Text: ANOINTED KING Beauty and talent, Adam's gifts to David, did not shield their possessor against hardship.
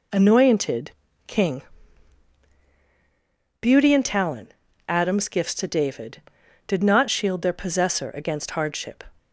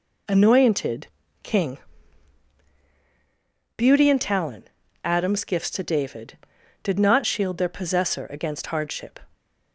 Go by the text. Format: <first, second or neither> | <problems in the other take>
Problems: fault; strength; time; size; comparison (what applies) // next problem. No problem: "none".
neither | pauses between "ANOINTED" and "KING"; slight; the same in both // pauses between "KING" and "Beauty"; strong; the same in both